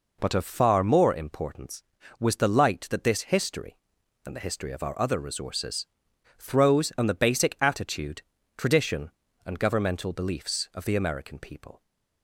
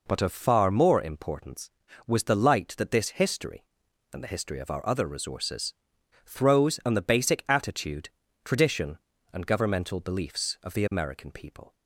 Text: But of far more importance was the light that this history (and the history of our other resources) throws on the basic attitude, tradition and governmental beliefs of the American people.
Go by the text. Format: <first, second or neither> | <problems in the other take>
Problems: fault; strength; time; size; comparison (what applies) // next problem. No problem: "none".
neither | none